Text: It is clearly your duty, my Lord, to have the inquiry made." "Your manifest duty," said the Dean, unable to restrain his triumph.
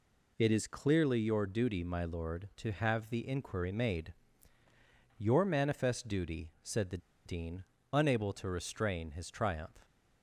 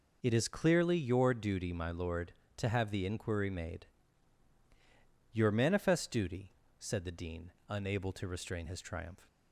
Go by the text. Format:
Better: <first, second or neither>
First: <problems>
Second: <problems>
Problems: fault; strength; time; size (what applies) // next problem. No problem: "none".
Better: second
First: pauses between "the" and "Dean"; slight; at 6.9 s; 0.27 s long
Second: none